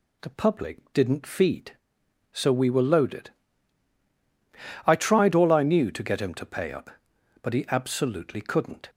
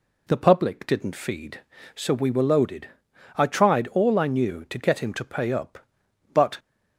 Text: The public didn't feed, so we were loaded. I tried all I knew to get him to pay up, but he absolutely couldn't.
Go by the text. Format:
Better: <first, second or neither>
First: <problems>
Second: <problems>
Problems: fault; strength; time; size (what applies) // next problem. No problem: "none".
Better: first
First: none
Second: stops before "he absolutely couldn't"; at 6.5 s